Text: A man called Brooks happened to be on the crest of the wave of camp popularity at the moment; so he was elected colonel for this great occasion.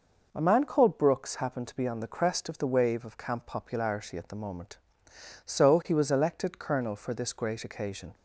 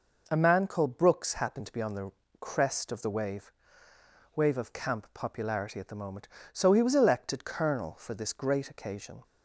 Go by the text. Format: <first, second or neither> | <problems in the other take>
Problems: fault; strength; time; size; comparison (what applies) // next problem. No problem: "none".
first | pauses between "the" and "crest"; slight; at 2.1 s; 0.30 s long // says "wave" twice; at 4.3 s